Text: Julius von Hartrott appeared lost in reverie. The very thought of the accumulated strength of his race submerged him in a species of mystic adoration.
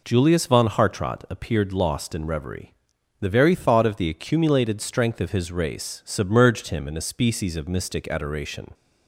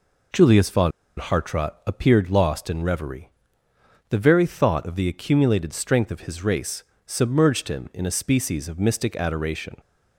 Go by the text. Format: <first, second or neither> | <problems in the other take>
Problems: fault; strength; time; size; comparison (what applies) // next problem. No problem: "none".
first | pauses between "von" and "Hartrott"; slight; at 0.9 s; 0.28 s long // pauses between "race" and "submerged"; slight; at 6.8 s; 0.24 s long